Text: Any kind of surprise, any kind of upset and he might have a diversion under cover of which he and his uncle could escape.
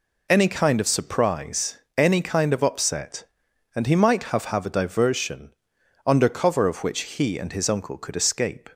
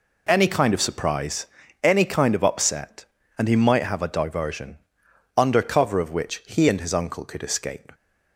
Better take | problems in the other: second | says "have" twice; at 4.4 s // pauses between "diversion" and "under"; noticeable; at 5.5 s; 0.56 s long; noticeable in the second

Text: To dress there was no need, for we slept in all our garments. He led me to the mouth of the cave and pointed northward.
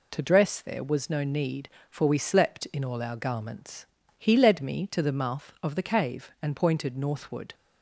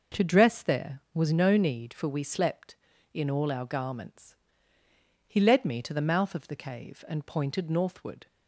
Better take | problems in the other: neither | none

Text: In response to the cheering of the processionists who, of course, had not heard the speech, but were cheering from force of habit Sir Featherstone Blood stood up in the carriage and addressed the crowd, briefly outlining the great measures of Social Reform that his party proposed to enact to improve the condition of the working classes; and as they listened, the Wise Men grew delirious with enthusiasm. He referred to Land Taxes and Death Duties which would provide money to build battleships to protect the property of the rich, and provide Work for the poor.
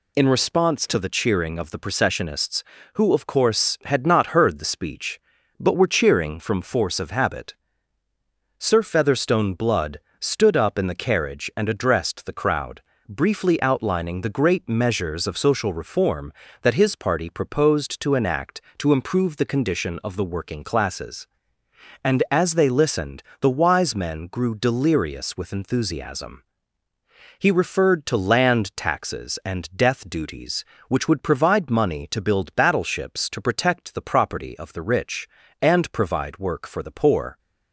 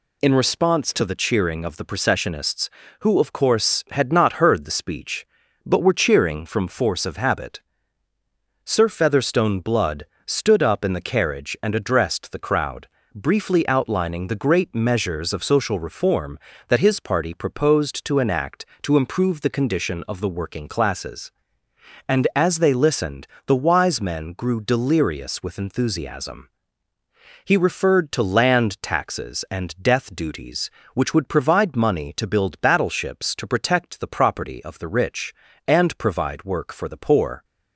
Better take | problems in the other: neither | pauses between "habit" and "Sir"; the same in both // pauses between "Blood" and "stood"; slight; the same in both

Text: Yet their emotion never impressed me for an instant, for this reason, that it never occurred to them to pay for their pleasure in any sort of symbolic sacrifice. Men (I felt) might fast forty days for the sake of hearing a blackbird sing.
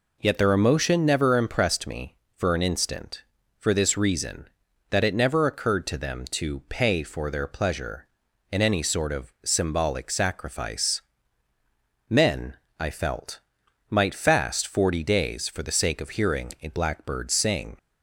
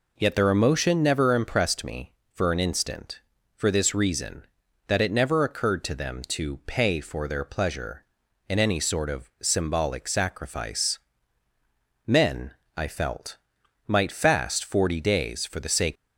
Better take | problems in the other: first | stops before "of hearing a blackbird sing"; at 15.9 s

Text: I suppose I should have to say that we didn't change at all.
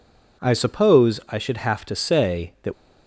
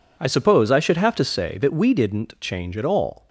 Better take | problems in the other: second | stops before "we didn't change at all"; at 2.7 s

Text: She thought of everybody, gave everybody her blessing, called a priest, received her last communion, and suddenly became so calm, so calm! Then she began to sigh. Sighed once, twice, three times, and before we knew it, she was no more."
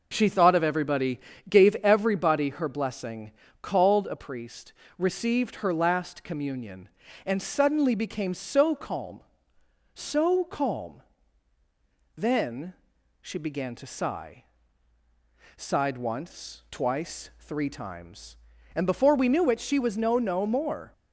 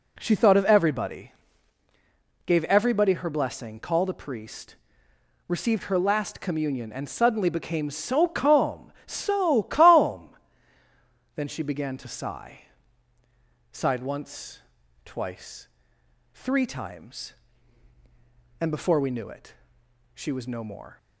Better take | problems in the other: second | pauses between "Then" and "she"; noticeable; at 12.7 s; 0.48 s long // says "no" twice; at 20.1 s

